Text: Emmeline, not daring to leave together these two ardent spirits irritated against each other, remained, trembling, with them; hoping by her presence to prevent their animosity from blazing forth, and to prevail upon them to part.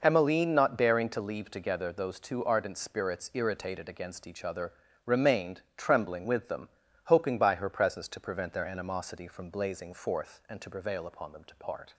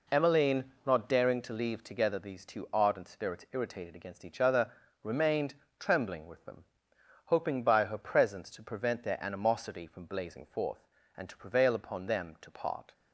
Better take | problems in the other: second | says "those" for "these"; at 1.9 s

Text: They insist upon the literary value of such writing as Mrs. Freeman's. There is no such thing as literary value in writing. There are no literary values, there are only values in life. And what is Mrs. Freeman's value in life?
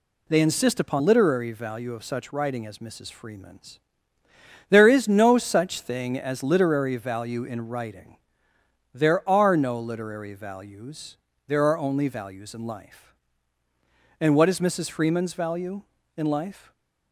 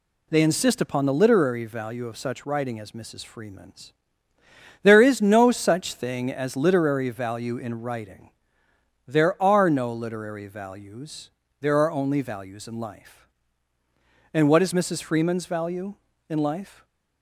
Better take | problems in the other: second | skips "the"; at 1.0 s // stays silent after the last word; slight; from 16.6 s on; 0.5 s long

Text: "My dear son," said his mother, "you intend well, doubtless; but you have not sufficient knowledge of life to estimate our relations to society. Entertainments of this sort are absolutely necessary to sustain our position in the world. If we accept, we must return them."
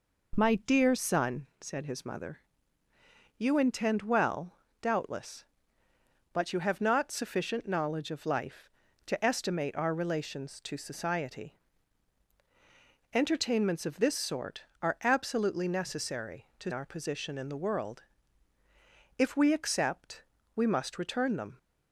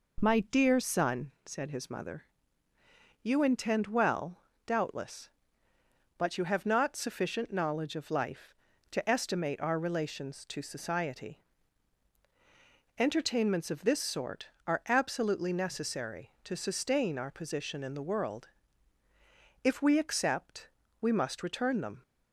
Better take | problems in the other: second | skips "sustain"; at 16.7 s

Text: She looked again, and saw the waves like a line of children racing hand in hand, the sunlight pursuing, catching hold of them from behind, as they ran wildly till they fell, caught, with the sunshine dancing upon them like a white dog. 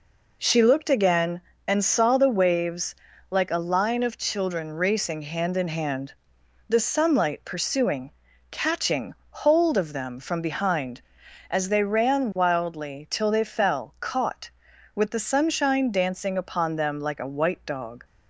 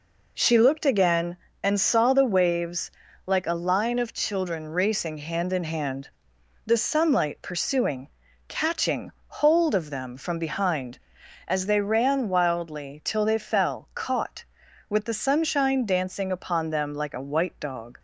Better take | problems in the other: neither | pauses between "waves" and "like"; slight; the same in both // pauses between "catching" and "hold"; slight; the same in both

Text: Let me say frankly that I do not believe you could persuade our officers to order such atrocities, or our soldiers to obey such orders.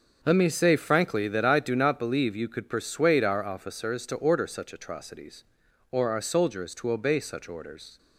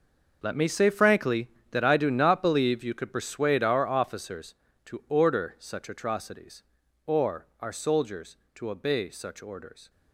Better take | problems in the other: first | gets quieter; strong; throughout; 15 dB // starts louder than the rest; noticeable; until 1.4 s; 6 dB; also in the first

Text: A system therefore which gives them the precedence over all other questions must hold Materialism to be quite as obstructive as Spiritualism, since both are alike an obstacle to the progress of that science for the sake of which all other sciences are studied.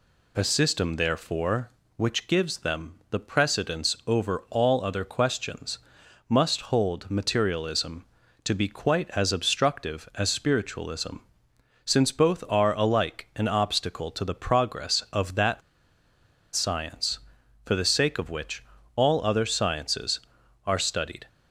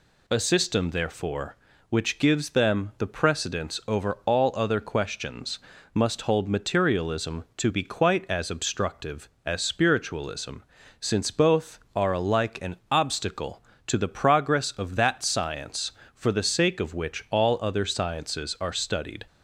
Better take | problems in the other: second | pauses between "questions" and "must"; noticeable; at 5.7 s; 0.50 s long; slight in the second // pauses between "that" and "science"; noticeable; at 15.6 s; 0.94 s long // pauses between "which" and "all"; slight; at 18.6 s; 0.32 s long

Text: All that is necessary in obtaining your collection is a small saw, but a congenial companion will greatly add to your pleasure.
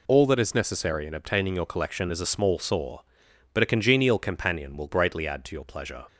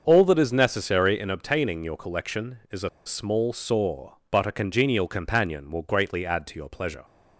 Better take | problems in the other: first | starts louder than the rest; until 1.0 s; 6.5 dB // pauses between "a" and "small"; slight; at 2.8 s; 0.17 s long

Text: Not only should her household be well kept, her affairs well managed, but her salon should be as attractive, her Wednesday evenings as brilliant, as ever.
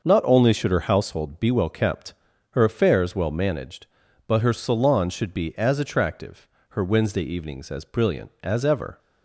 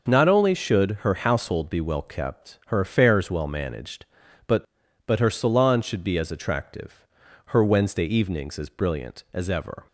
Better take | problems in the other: first | starts louder than the rest; noticeable; until 1.1 s; 6 dB; noticeable in the first // says "but" twice; at 5.0 s

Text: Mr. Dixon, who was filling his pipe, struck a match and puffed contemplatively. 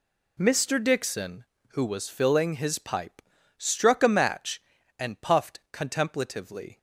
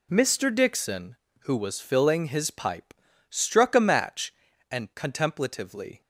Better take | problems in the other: first | skips "puffed"; at 4.9 s

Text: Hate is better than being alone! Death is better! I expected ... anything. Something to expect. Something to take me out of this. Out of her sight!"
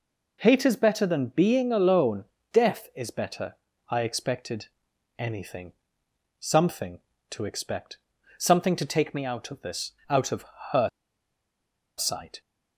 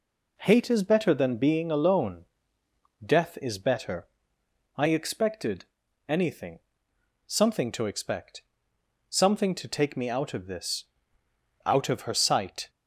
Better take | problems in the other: second | pauses between "of" and "her"; slight; at 10.4 s; 0.26 s long // pauses between "her" and "sight"; at 10.8 s; 1.1 s long

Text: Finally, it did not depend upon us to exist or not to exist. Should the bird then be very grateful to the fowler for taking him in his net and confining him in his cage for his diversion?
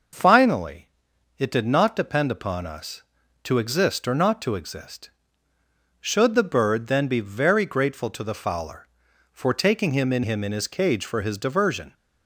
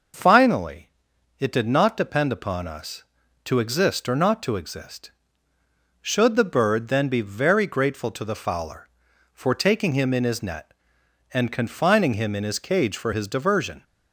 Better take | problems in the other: second | skips "his net and confining"; at 10.2 s

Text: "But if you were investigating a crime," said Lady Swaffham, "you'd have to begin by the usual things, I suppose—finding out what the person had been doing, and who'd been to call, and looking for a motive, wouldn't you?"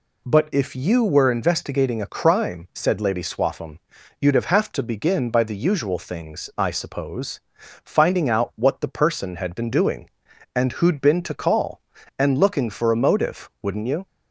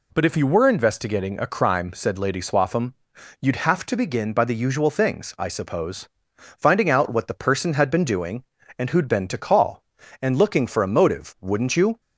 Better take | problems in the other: second | says "have" twice; at 4.4 s

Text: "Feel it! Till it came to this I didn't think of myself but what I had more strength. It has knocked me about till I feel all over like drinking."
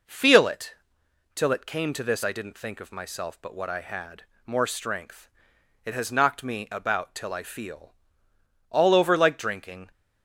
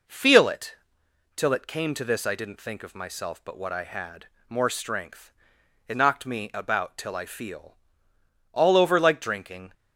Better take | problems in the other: first | pauses between "had" and "more"; slight; at 4.2 s; 0.20 s long; slight in the first // skips "has"; at 5.9 s // pauses between "feel" and "all"; noticeable; at 7.7 s; 0.74 s long; noticeable in the first

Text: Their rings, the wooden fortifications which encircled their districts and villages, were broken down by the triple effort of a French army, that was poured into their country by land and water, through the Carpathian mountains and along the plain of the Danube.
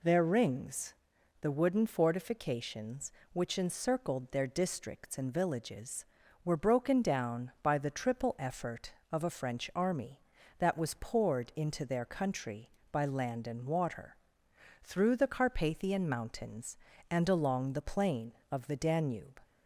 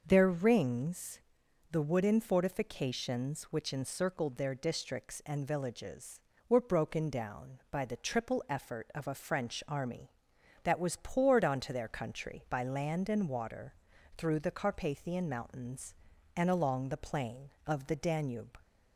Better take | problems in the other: first | starts louder than the rest; noticeable; until 1.0 s; 6 dB // says "onto" for "into"; at 11.4 s

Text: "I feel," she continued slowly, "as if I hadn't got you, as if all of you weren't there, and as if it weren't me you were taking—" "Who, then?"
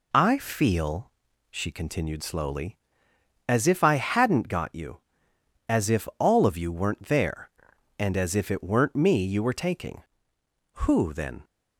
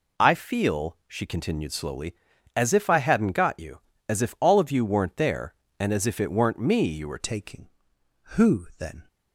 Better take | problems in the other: first | changes voice at "taking"; from 7.1 s on; 1.9 s long

